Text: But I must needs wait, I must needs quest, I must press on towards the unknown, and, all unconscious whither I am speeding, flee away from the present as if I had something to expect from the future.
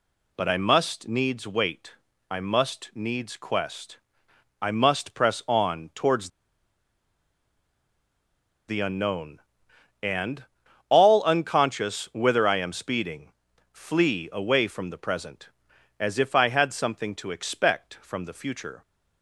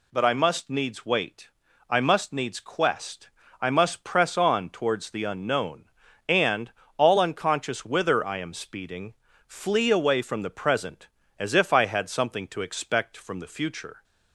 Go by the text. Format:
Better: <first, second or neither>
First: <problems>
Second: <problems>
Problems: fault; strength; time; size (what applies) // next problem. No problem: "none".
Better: second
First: pauses between "towards" and "the"; strong; at 6.2 s; 2.4 s long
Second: none